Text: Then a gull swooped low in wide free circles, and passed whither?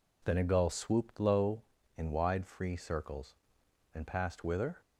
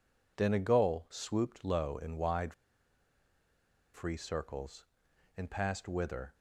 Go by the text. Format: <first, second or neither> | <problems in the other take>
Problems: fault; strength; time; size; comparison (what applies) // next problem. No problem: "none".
first | pauses between "wide" and "free"; strong; at 2.5 s; 1.4 s long